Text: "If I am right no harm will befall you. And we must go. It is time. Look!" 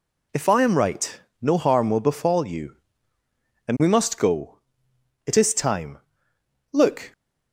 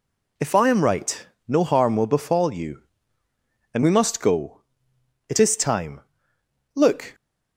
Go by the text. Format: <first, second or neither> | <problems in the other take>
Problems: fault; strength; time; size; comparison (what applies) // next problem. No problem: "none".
neither | pauses between "right" and "no"; slight; the same in both